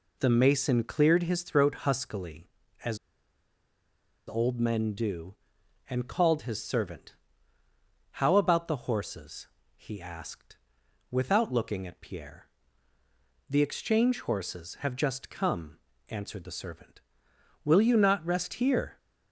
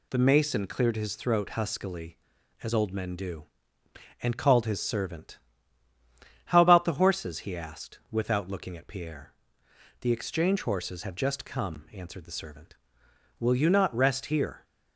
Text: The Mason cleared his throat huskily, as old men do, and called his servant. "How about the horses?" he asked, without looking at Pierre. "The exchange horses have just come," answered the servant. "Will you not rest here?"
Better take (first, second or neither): second